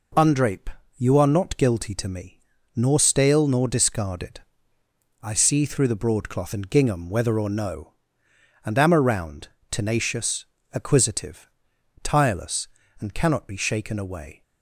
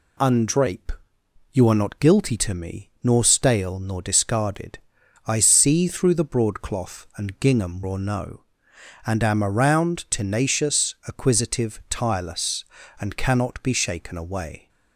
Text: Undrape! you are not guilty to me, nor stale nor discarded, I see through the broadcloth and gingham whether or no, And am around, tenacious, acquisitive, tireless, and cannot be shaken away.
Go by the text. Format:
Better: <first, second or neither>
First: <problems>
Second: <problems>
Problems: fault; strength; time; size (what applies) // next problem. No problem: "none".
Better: first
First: none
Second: skips "whether"; at 7.8 s